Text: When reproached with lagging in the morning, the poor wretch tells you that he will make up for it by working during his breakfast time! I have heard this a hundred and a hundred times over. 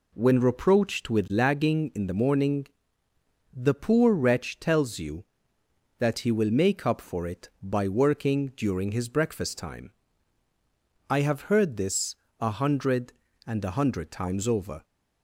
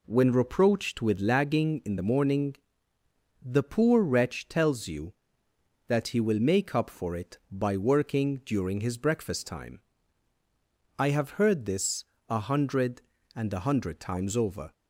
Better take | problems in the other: neither | pauses between "this" and "a"; slight; the same in both

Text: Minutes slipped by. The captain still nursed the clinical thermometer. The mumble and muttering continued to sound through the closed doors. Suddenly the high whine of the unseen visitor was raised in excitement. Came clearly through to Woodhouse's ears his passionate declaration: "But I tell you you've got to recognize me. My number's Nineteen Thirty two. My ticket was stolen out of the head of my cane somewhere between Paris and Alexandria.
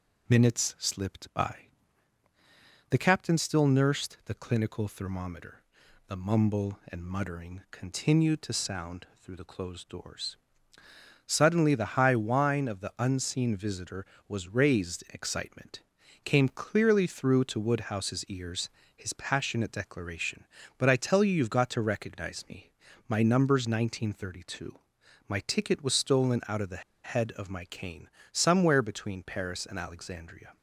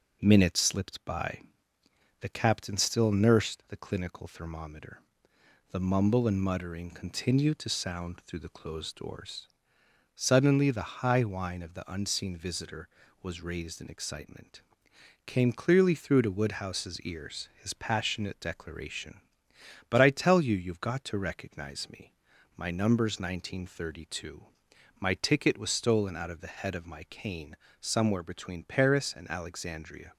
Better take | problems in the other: second | pauses between "ears" and "his"; slight; at 18.6 s; 0.28 s long // pauses between "the" and "head"; slight; at 26.8 s; 0.21 s long // pauses between "cane" and "somewhere"; slight; at 28.0 s; 0.24 s long; slight in the second

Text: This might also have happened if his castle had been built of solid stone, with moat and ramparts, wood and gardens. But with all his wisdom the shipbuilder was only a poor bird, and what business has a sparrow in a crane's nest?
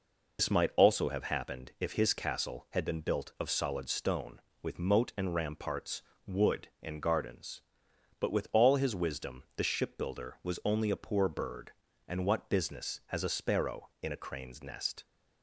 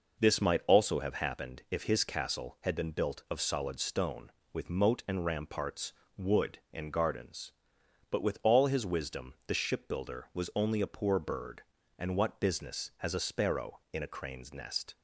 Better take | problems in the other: second | loses the start of "This"; at 0.3 s; 110 ms

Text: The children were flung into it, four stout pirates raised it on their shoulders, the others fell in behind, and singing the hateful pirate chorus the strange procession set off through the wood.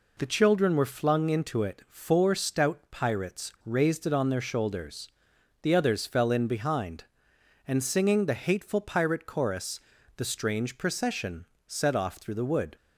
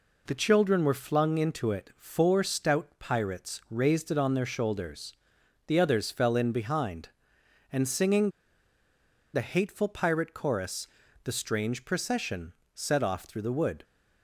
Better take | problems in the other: first | pauses between "singing" and "the"; at 8.3 s; 1.0 s long // pauses between "chorus" and "the"; at 10.8 s; 0.38 s long; also in the first // pauses between "procession" and "set"; slight; at 12.5 s; 0.20 s long; slight in the first

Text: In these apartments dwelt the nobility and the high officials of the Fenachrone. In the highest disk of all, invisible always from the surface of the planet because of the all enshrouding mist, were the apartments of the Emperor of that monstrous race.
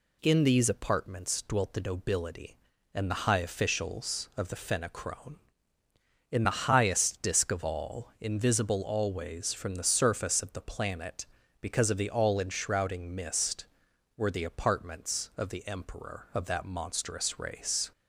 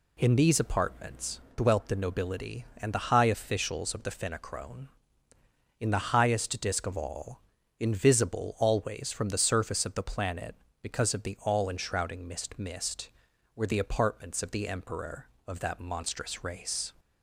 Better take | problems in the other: first | says "mist" twice; at 12.5 s

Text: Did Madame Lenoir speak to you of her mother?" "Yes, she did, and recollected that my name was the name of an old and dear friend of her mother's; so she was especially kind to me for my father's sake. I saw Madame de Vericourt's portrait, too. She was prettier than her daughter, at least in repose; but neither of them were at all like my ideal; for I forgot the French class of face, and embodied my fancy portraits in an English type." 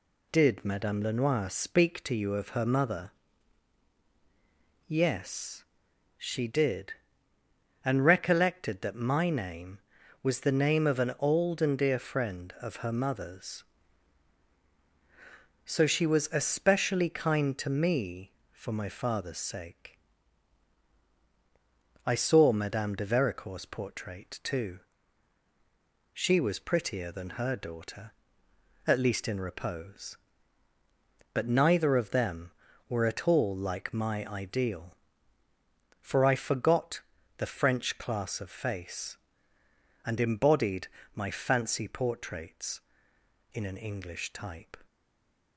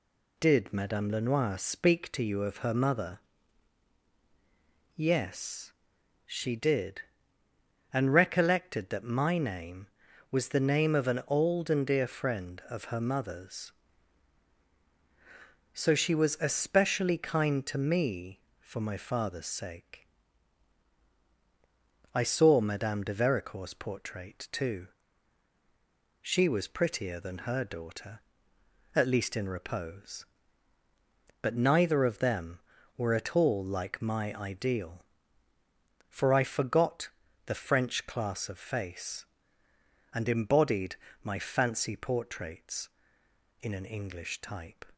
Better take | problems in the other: second | pauses between "forgot" and "the"; slight; at 37.0 s; 0.36 s long; slight in the second // pauses between "embodied" and "my"; slight; at 40.8 s; 0.28 s long; slight in the second // stays silent after the last word; slight; from 44.8 s on; 0.7 s long

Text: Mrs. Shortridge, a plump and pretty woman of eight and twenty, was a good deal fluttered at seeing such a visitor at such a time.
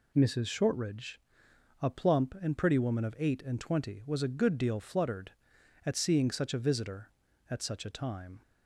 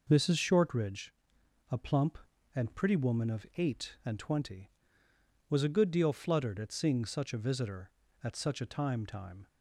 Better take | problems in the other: first | says "time" twice; at 9.0 s

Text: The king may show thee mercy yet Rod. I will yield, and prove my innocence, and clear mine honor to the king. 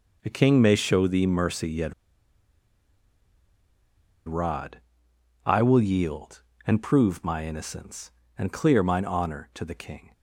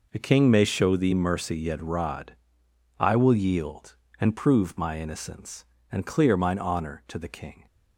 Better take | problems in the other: second | pauses between "yet" and "Rod"; strong; at 1.9 s; 2.3 s long

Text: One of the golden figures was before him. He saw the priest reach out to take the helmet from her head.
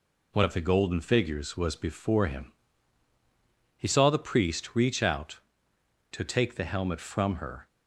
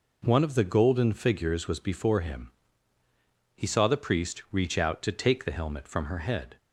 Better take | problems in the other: second | stops before "head"; at 7.6 s

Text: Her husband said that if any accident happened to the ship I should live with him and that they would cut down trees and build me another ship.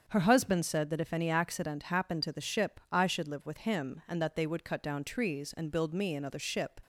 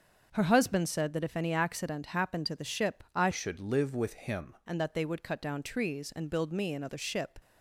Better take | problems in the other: first | starts louder than the rest; until 1.3 s; 6.5 dB; also in the first // changes voice from "should" to "him"; from 3.3 to 4.5 s; 1.2 s long

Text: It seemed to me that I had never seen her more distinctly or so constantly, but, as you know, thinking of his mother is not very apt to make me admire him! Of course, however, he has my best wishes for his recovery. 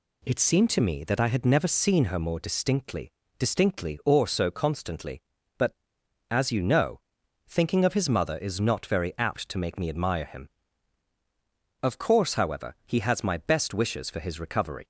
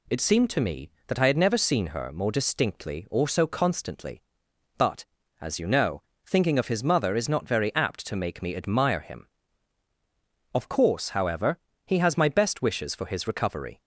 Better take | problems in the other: second | says "distinctly" twice; at 3.3 s

